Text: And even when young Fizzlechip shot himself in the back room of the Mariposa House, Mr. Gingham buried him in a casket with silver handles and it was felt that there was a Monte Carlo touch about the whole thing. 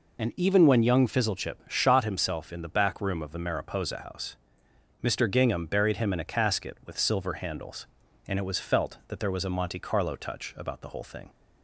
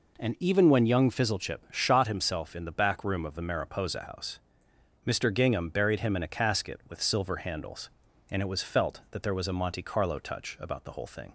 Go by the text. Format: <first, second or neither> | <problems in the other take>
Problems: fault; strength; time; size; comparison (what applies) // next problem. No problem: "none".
second | loses the start of "And"; at 0.1 s; 70 ms